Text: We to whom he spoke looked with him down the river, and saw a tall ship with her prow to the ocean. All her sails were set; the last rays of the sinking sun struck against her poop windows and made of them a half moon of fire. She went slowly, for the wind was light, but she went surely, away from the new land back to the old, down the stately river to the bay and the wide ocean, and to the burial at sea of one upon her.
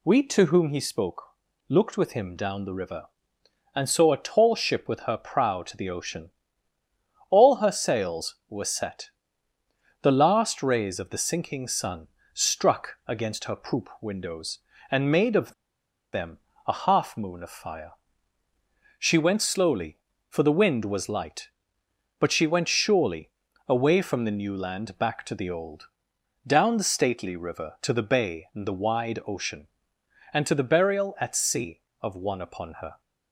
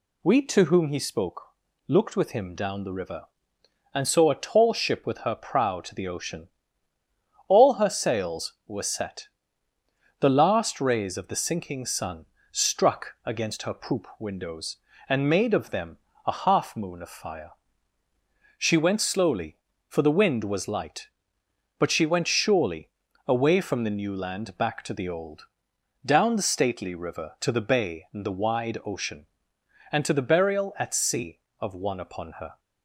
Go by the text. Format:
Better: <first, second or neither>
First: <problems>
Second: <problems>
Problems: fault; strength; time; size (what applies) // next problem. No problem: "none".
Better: second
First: pauses between "spoke" and "looked"; noticeable; at 1.2 s; 0.48 s long // pauses between "sun" and "struck"; slight; at 12.0 s; 0.26 s long // pauses between "of" and "them"; noticeable; at 15.5 s; 0.61 s long // pauses between "them" and "a"; slight; at 16.3 s; 0.30 s long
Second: pauses between "spoke" and "looked"; noticeable; at 1.4 s; 0.48 s long // pauses between "sun" and "struck"; slight; at 12.2 s; 0.26 s long // pauses between "them" and "a"; slight; at 15.9 s; 0.30 s long